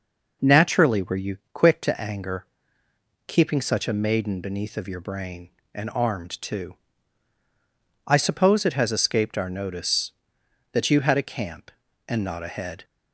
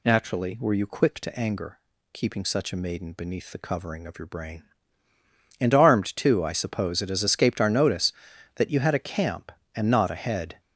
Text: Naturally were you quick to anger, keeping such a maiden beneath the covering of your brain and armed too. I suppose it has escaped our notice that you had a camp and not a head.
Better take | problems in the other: second | pauses between "you" and "quick"; slight; at 1.3 s; 0.16 s long // skips "the covering"; at 4.7 s

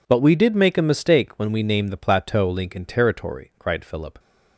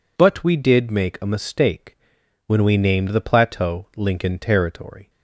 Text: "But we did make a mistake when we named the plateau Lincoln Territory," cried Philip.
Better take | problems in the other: first | pauses between "mistake" and "when"; noticeable; at 1.9 s; 0.48 s long // stops before "cried Philip"; at 5.0 s

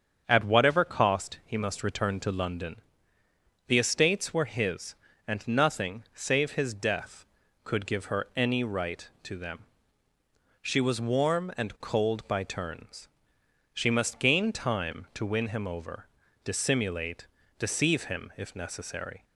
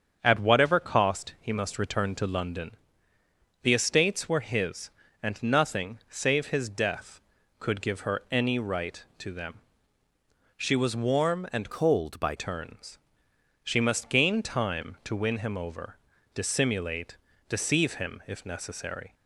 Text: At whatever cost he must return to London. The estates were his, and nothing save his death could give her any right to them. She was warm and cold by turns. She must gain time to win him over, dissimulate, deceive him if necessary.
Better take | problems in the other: first | starts louder than the rest; strong; until 1.2 s; 7 dB; strong in the first // changes voice from "cold" to "by"; from 11.7 to 12.3 s; 0.6 s long

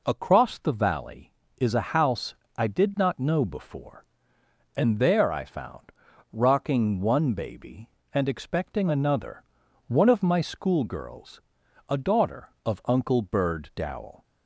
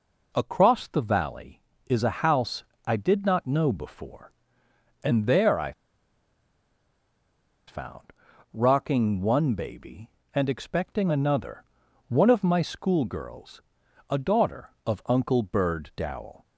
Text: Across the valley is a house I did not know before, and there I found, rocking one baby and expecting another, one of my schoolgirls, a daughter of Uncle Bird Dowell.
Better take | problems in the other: first | pauses between "house" and "I"; slight; at 2.6 s; 0.22 s long; slight in the first // pauses between "I" and "found"; strong; at 5.7 s; 1.9 s long

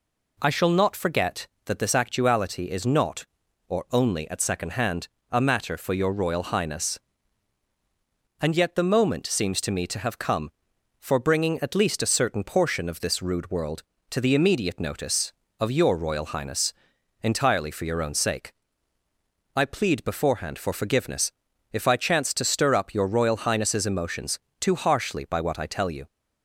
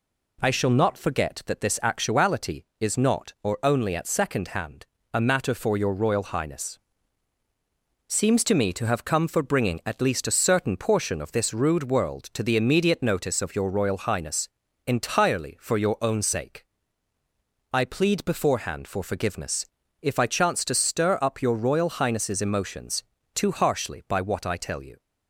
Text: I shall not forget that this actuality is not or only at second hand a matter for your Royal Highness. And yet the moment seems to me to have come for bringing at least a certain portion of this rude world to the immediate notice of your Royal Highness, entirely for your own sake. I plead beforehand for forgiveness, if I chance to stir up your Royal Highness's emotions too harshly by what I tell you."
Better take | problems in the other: first | pauses between "hand" and "a"; slight; at 4.8 s; 0.26 s long; slight in the first // skips "And yet the moment"; at 7.4 s // pauses between "emotions" and "too"; slight; at 23.0 s; 0.30 s long; slight in the first

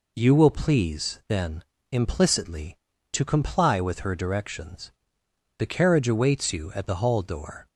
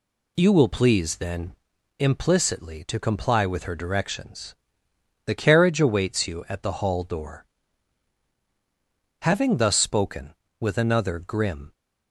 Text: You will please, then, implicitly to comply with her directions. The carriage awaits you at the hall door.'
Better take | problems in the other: first | goes on to say "Having thus spoken with another grim"; strong; from 9.2 s on; 2.5 s long

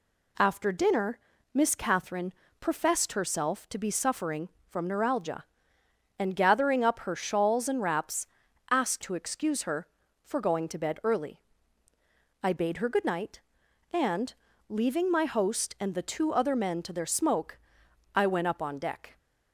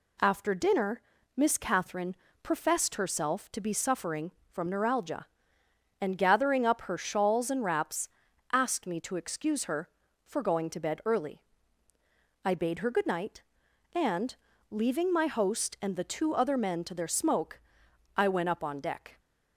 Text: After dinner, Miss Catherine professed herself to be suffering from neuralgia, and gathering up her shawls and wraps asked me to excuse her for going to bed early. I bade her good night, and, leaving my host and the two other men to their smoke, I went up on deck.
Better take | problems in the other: second | pauses between "Catherine" and "professed"; slight; at 2.3 s; 0.26 s long; slight in the second // pauses between "wraps" and "asked"; at 8.2 s; 0.42 s long; also in the second // skips "me"; at 9.0 s

